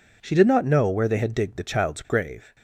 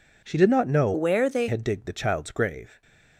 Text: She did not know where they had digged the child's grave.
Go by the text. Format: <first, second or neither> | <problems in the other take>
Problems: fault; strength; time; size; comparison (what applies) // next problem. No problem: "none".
first | changes voice from "where" to "they"; from 0.9 to 1.4 s; 0.5 s long // stays silent after the last word; slight; from 2.6 s on; 0.5 s long